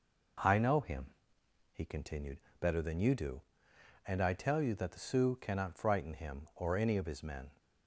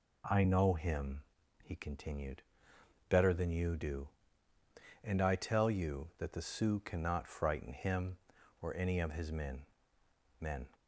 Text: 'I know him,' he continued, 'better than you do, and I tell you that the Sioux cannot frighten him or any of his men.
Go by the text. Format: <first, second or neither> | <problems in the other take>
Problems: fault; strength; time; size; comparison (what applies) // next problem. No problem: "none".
first | says "men" twice; at 10.4 s